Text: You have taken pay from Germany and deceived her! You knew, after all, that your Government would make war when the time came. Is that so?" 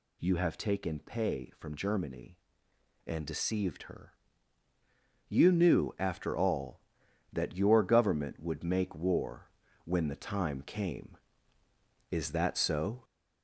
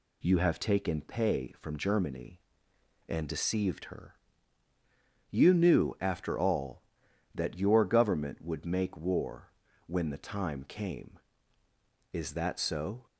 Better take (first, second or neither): second